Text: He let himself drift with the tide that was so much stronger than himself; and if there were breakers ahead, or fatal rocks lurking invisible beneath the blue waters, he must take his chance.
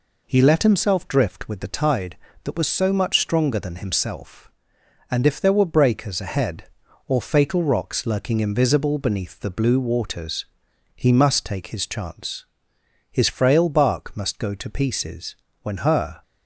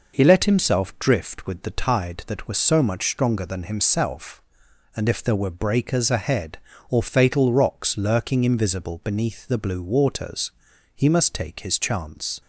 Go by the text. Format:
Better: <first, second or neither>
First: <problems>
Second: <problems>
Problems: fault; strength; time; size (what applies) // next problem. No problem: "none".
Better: second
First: goes on to say "His frail bark must go to pieces when her"; strong; from 13.1 s on; 3.1 s long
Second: none